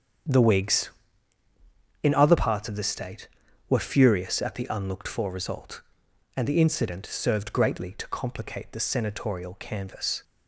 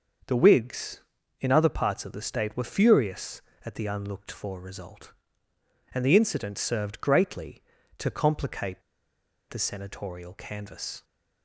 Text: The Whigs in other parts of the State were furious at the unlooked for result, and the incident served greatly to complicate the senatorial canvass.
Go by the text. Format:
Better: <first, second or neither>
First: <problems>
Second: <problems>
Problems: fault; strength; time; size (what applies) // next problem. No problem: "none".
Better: first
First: starts louder than the rest; strong; until 2.4 s; 8 dB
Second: starts louder than the rest; until 1.6 s; 6.5 dB // pauses between "complicate" and "the"; noticeable; at 8.8 s; 0.68 s long